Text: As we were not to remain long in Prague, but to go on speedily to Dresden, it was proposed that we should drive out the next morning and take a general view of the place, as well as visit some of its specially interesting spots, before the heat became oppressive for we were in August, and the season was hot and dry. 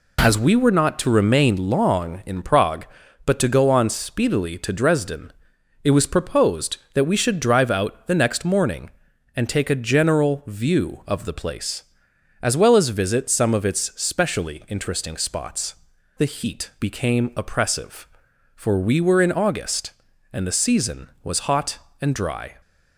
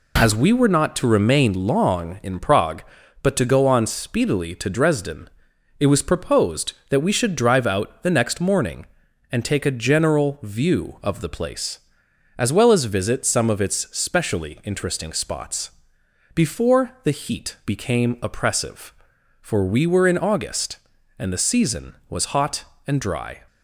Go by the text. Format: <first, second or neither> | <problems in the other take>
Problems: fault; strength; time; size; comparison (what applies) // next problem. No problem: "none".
second | skips "before"; at 15.9 s